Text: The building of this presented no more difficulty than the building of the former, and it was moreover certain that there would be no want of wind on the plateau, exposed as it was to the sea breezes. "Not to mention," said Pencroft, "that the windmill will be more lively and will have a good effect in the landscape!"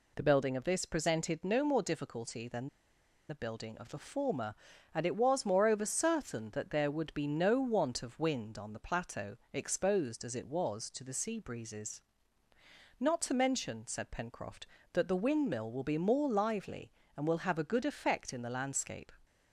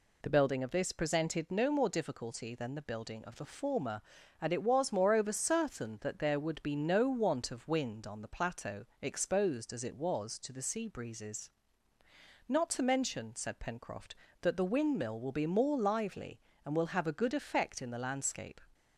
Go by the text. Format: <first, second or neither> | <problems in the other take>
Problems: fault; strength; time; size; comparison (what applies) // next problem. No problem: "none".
second | pauses between "than" and "the"; noticeable; at 2.6 s; 0.61 s long